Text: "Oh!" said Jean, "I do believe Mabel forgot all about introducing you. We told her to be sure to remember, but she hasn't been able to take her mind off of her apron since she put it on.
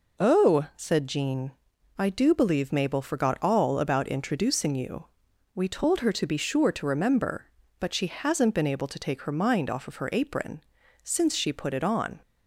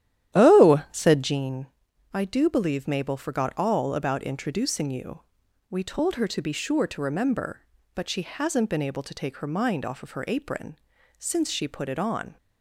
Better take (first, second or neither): first